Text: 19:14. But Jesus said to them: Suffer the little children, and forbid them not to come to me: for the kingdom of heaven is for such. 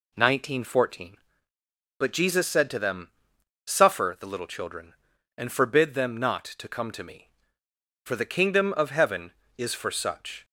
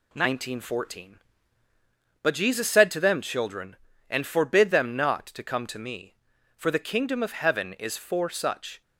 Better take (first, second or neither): first